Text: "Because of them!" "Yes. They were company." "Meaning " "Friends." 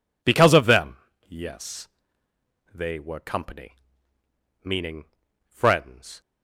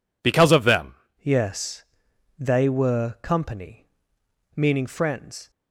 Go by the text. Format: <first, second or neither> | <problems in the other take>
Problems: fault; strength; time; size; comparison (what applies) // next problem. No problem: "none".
first | changes voice at "Yes"; from 1.2 s on; 4.2 s long